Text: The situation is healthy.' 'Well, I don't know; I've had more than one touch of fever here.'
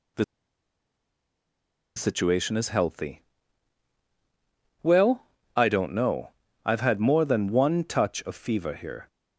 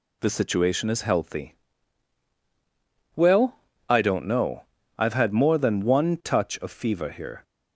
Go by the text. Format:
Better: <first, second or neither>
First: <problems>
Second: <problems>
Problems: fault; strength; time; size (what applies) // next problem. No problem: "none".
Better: second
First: pauses between "The" and "situation"; strong; at 0.2 s; 1.7 s long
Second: none